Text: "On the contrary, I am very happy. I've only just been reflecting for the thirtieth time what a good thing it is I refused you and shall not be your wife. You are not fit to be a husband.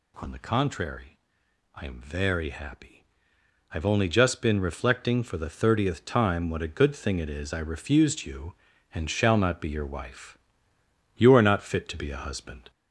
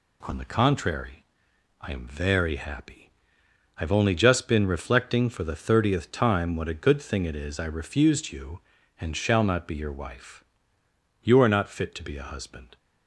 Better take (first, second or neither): second